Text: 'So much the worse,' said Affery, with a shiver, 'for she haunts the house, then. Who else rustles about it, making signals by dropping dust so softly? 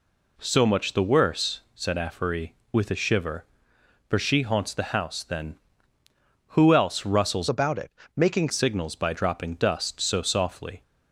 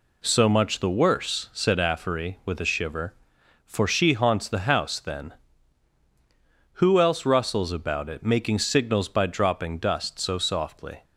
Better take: second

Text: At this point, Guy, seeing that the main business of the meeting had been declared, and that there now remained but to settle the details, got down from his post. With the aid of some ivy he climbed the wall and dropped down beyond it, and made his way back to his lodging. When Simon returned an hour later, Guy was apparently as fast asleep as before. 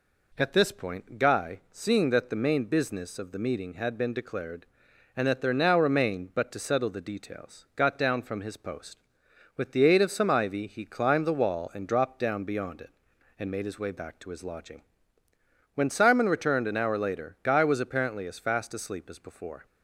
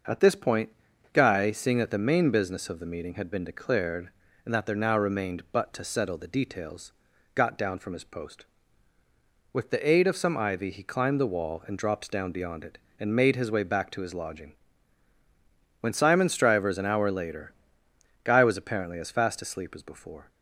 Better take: first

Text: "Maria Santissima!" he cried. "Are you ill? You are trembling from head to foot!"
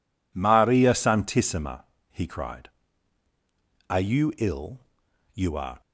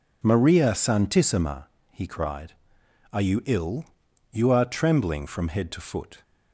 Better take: second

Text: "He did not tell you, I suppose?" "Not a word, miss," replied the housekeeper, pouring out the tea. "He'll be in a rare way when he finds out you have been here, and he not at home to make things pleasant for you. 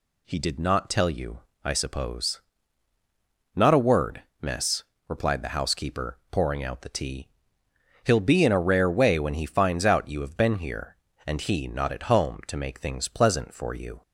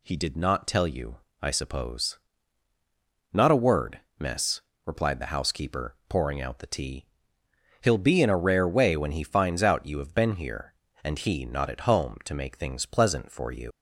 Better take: first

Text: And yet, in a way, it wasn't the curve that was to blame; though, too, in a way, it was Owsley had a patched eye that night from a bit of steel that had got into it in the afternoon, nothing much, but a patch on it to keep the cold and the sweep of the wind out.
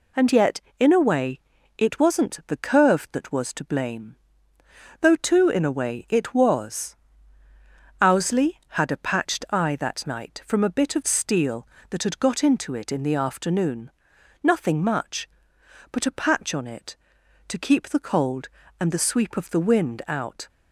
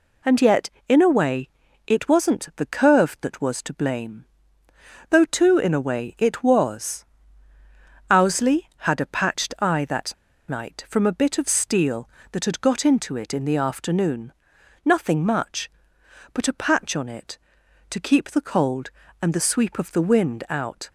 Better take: first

